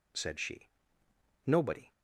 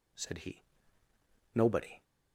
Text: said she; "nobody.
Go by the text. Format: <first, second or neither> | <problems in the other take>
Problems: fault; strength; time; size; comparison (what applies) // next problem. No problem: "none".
first | says "he" for "she"; at 0.3 s